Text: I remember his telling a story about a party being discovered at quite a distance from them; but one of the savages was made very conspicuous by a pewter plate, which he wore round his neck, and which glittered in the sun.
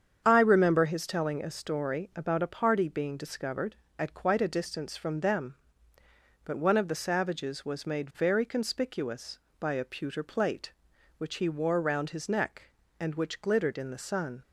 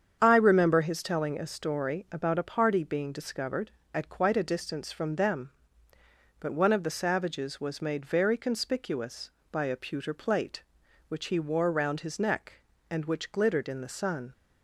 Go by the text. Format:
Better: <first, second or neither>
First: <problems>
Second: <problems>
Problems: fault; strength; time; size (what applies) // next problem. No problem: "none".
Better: neither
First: starts louder than the rest; strong; until 1.2 s; 7.5 dB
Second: starts louder than the rest; strong; until 1.2 s; 7.5 dB